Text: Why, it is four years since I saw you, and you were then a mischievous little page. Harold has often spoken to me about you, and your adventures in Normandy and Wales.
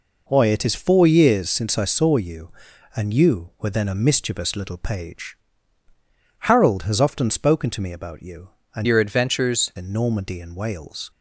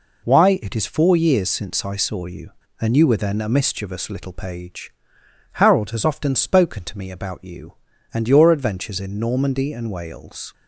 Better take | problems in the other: second | changes voice from "your" to "adventures"; from 8.8 to 9.7 s; 0.9 s long

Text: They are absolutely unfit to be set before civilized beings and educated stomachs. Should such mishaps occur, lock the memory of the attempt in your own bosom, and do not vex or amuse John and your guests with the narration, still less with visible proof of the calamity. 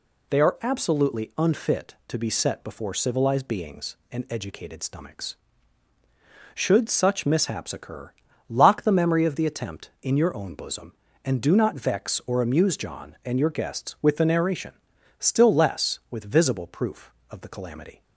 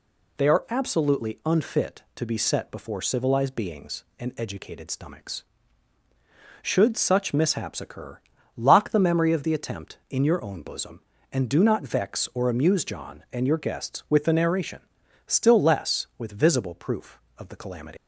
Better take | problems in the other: first | leaves "calamity" unfinished; at 17.9 s; 130 ms

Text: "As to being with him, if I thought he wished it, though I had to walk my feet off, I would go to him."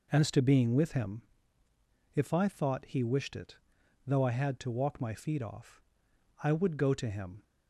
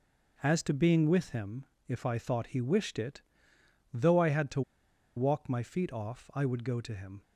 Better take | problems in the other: first | pauses between "to" and "walk"; noticeable; at 4.6 s; 0.55 s long

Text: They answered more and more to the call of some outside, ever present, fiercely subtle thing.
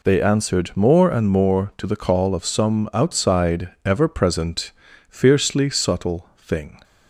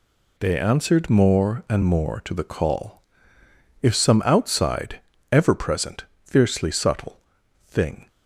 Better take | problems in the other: first | says "if" for "of"; at 3.8 s // pauses between "subtle" and "thing"; noticeable; at 7.1 s; 0.48 s long

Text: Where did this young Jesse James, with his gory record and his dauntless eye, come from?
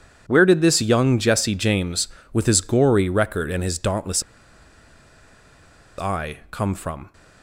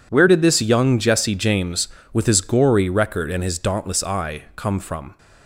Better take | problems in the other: second | pauses between "dauntless" and "eye"; strong; at 4.2 s; 1.7 s long

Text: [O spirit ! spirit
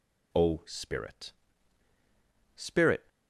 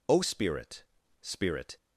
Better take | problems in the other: neither | none

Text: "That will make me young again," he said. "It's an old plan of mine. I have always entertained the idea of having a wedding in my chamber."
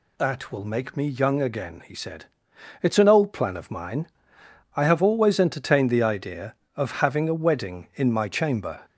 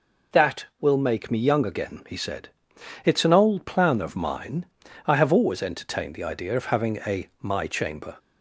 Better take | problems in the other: first | skips "wedding in"; at 7.3 s

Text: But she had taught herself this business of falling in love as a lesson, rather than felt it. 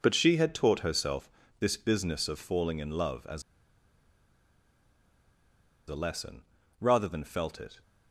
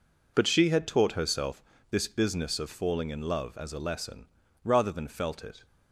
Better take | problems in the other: second | pauses between "herself" and "this"; slight; at 1.2 s; 0.30 s long; slight in the second // pauses between "as" and "a"; strong; at 3.4 s; 2.4 s long

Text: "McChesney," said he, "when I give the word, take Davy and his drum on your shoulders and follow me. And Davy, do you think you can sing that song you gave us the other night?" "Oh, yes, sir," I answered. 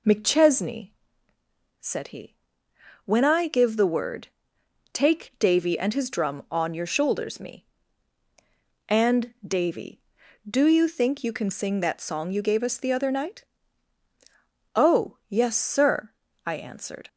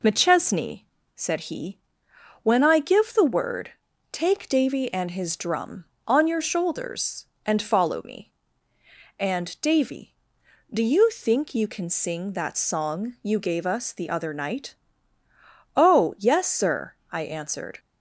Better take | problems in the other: second | skips "and follow"; at 7.3 s

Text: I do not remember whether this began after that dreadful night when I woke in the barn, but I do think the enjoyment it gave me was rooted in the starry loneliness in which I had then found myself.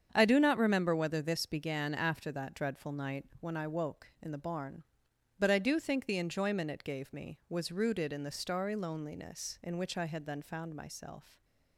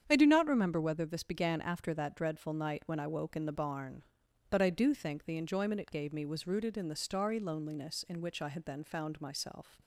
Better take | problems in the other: neither | starts louder than the rest; strong; the same in both

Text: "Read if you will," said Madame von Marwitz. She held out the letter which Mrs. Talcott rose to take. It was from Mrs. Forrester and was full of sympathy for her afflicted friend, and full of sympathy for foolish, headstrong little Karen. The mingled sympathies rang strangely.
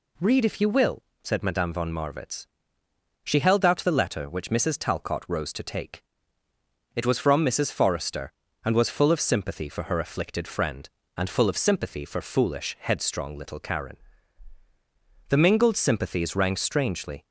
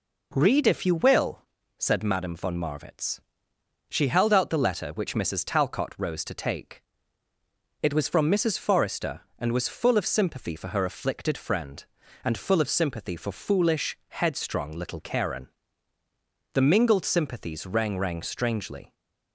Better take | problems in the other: first | says "rang" twice; at 17.9 s

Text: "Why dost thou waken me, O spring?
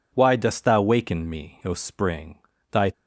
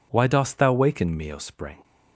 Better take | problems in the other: second | goes on to say "Thy"; slight; from 2.7 s on; 0.22 s long

